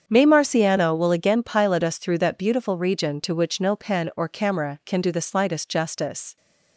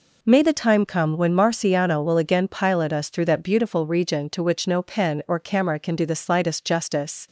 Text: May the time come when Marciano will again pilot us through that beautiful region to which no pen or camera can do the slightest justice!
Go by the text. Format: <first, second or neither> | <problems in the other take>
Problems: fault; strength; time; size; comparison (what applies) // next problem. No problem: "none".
second | starts louder than the rest; strong; until 1.0 s; 7.5 dB // skips "the time come when"; at 0.2 s